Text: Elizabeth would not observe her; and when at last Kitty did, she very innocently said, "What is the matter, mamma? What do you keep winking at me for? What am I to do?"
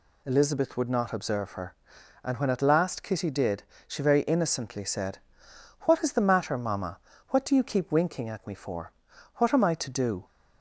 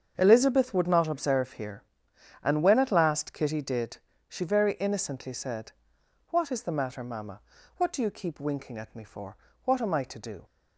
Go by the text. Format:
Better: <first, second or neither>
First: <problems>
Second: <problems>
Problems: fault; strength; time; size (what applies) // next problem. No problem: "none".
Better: first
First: none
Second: starts louder than the rest; strong; until 1.1 s; 7.5 dB // says "here" for "her"; at 1.5 s